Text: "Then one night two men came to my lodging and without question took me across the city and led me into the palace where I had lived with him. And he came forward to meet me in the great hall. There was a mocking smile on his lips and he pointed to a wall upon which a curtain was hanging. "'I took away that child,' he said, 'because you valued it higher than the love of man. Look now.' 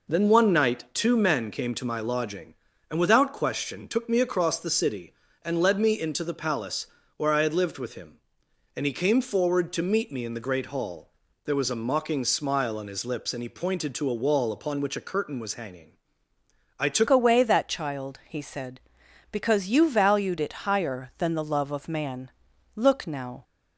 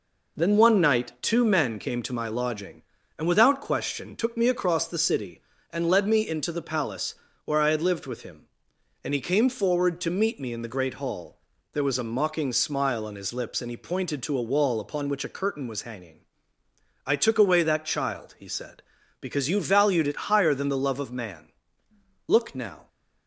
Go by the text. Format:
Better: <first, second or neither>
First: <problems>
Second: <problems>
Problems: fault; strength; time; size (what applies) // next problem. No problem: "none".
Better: second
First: pauses between "palace" and "where"; slight; at 6.8 s; 0.30 s long // changes voice at "away"; from 17.0 s on; 6.4 s long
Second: pauses between "palace" and "where"; slight; at 7.1 s; 0.30 s long